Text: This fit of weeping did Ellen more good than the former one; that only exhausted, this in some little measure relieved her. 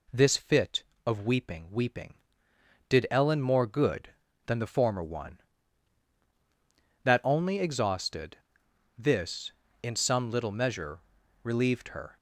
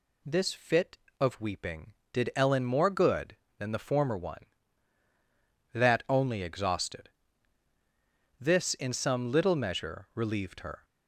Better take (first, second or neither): second